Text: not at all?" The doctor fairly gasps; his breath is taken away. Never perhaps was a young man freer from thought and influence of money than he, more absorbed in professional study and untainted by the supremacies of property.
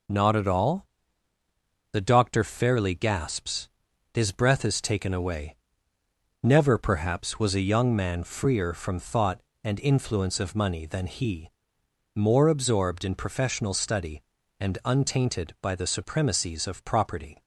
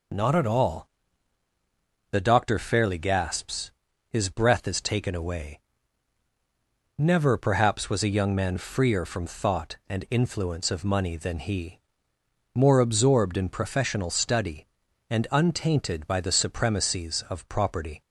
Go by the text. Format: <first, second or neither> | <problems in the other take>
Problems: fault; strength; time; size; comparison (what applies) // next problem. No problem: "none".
neither | none